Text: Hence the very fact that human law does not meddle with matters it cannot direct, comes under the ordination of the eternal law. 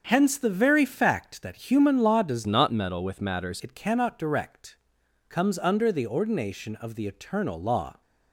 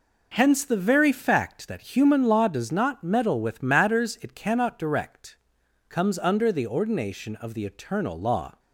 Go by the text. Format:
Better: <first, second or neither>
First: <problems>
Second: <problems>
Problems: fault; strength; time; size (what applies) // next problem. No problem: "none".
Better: second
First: starts louder than the rest; until 1.0 s; 7 dB // changes voice from "not" to "matters"; from 2.4 to 3.6 s; 1.2 s long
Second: none